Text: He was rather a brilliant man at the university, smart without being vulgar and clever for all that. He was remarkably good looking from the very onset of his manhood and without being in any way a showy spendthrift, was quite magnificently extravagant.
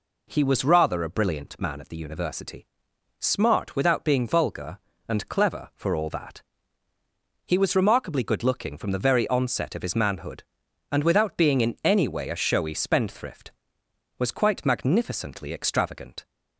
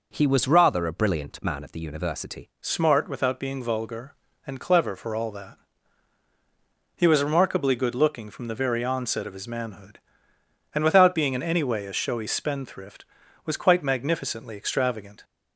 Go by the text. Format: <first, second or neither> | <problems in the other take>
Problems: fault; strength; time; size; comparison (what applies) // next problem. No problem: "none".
first | changes voice at "smart"; from 2.5 s on; 12.7 s long